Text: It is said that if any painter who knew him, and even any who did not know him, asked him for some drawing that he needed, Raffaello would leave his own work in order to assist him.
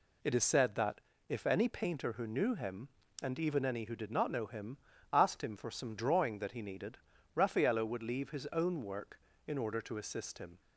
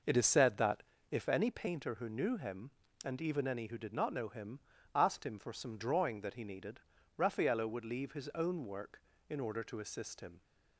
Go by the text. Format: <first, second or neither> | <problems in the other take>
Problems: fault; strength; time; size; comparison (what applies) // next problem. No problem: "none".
first | starts louder than the rest; noticeable; until 1.4 s; 5.5 dB // pauses between "that" and "if"; slight; at 0.8 s; 0.28 s long; slight in the first